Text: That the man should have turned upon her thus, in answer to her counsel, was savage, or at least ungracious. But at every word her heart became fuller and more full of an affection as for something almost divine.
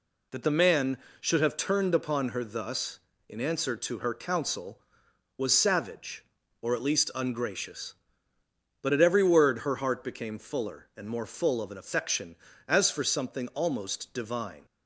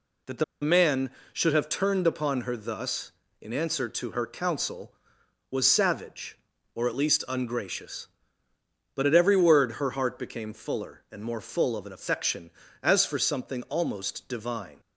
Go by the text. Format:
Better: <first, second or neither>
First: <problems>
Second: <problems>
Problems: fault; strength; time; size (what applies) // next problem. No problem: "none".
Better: first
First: none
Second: pauses between "the" and "man"; slight; at 0.4 s; 0.19 s long